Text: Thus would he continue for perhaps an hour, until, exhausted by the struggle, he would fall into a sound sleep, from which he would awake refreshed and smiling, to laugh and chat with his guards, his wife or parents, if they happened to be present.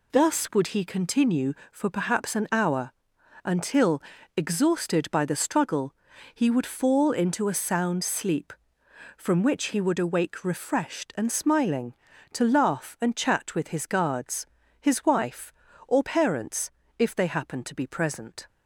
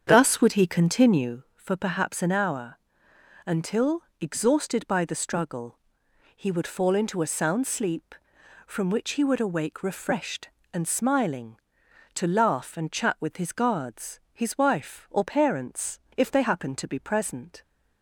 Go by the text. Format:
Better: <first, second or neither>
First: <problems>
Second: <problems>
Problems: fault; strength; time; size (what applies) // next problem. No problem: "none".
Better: first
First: none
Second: starts louder than the rest; strong; until 1.6 s; 8 dB